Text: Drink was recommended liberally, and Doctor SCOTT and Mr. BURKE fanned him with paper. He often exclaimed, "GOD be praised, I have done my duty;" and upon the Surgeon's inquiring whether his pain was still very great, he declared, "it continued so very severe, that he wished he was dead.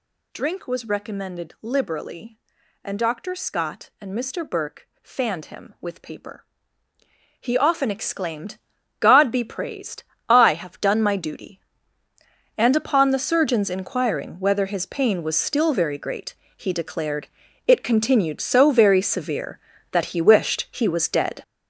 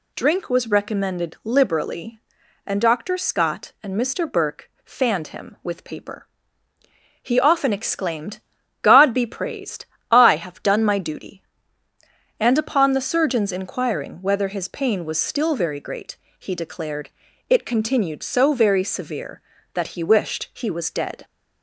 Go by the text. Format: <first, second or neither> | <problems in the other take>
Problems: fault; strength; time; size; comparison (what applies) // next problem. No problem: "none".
second | gets louder; strong; throughout; 9.5 dB // pauses between "BURKE" and "fanned"; slight; at 4.8 s; 0.16 s long; slight in the second